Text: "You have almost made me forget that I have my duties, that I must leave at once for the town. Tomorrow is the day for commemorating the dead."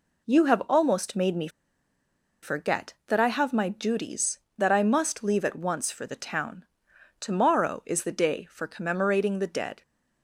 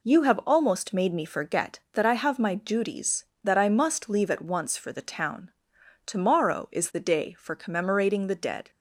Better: second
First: pauses between "me" and "forget"; noticeable; at 1.4 s; 0.94 s long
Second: none

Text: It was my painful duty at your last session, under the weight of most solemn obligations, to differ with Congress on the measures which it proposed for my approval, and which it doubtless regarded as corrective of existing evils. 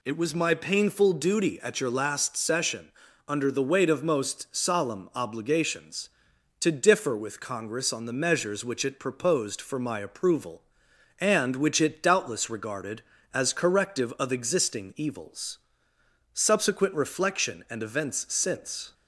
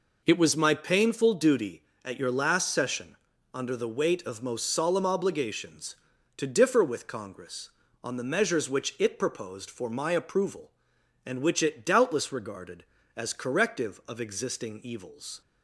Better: second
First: goes on to say "Subsequent reflection and events since"; strong; from 16.3 s on; 2.6 s long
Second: none

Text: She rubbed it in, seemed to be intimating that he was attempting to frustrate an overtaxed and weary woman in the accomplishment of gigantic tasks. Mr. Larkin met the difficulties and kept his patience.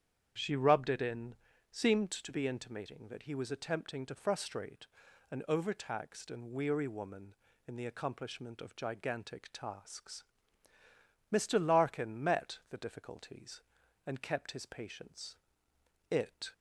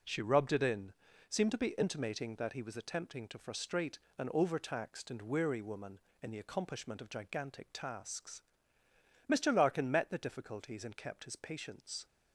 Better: second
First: starts louder than the rest; strong; until 1.7 s; 8.5 dB // pauses between "frustrate" and "an"; noticeable; at 4.8 s; 0.46 s long // goes on to say "It"; slight; from 16.1 s on; 0.42 s long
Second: pauses between "frustrate" and "an"; slight; at 3.9 s; 0.22 s long

